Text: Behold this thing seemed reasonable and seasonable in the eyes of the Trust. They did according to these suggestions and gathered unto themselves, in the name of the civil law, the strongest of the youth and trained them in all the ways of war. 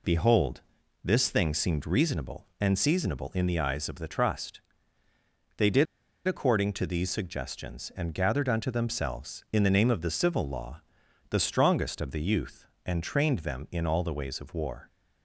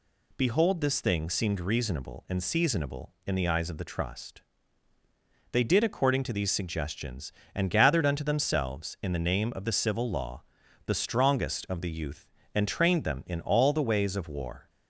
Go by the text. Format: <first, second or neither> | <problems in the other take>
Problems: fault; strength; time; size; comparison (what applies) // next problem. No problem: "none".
second | pauses between "Behold" and "this"; at 0.6 s; 0.42 s long // pauses between "did" and "according"; at 5.8 s; 0.41 s long